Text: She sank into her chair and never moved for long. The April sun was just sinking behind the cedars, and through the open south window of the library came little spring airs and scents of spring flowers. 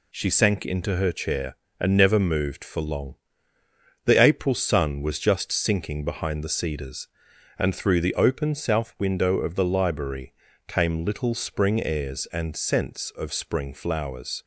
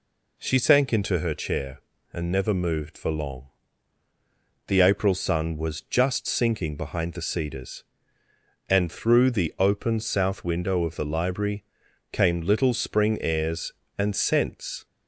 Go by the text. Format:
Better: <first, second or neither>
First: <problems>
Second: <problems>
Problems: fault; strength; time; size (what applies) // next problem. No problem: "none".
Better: first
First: pauses between "library" and "came"; slight; at 10.3 s; 0.34 s long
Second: pauses between "library" and "came"; noticeable; at 11.6 s; 0.48 s long // stops before "of spring flowers"; at 14.8 s